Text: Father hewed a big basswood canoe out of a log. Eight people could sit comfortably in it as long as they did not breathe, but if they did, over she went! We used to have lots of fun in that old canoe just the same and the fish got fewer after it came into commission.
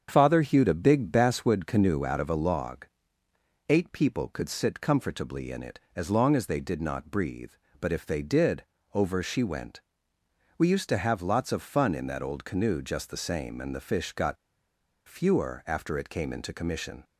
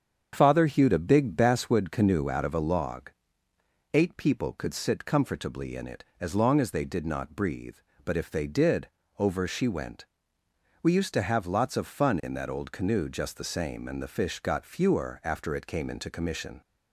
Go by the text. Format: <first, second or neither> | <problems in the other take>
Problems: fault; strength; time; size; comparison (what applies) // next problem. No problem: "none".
second | starts louder than the rest; strong; until 1.1 s; 7.5 dB; strong in the second // pauses between "got" and "fewer"; noticeable; at 14.3 s; 0.71 s long